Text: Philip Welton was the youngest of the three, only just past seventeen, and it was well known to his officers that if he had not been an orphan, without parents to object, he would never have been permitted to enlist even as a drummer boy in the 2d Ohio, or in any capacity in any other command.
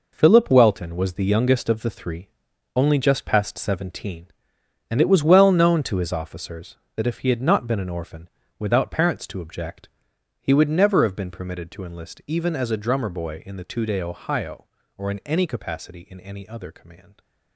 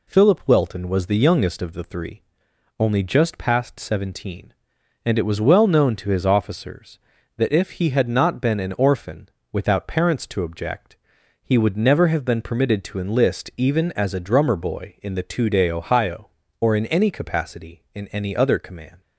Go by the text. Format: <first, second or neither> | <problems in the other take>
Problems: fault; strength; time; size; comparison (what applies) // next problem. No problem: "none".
second | gets quieter; strong; throughout; 10 dB